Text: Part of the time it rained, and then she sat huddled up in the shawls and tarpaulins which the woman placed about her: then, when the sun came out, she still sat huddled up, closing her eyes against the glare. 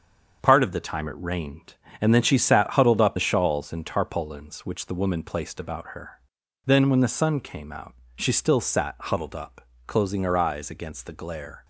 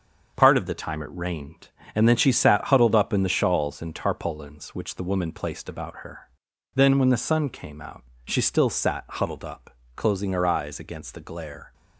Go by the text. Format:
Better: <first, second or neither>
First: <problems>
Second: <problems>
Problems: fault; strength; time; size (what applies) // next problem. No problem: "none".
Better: second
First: starts louder than the rest; until 1.4 s; 6.5 dB // skips "in"; at 3.1 s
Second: starts louder than the rest; until 1.3 s; 6.5 dB